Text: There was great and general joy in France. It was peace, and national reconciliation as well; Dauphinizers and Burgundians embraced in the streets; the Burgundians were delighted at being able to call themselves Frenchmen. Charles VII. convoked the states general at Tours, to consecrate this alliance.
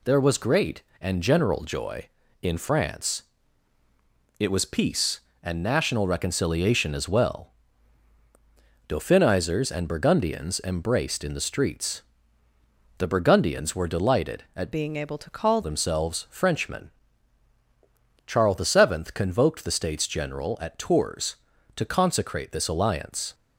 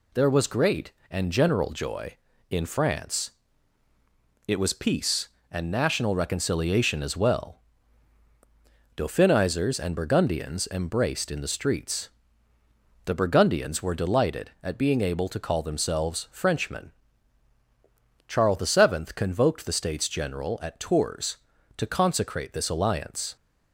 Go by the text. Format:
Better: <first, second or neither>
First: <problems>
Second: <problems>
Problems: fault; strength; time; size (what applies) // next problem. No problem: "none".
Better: second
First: changes voice from "being" to "call"; from 14.7 to 15.6 s; 0.9 s long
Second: none